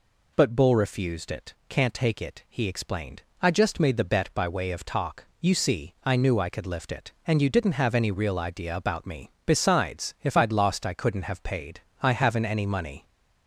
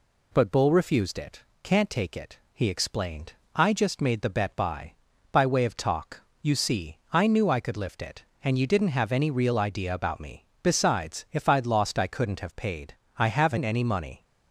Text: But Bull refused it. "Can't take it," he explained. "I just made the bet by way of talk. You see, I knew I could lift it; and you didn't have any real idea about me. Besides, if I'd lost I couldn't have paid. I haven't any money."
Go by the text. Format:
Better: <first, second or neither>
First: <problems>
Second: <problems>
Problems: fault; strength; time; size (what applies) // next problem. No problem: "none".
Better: first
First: none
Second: says "by" twice; at 5.3 s